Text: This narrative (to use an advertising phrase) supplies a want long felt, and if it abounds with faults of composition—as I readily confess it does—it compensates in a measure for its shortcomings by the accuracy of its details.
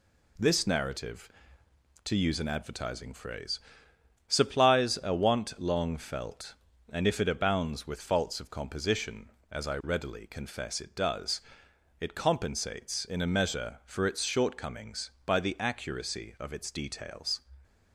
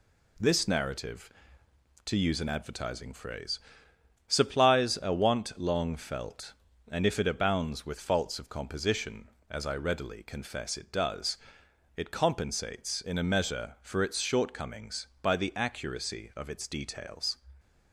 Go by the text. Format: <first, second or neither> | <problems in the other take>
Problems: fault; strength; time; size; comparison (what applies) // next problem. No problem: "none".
neither | none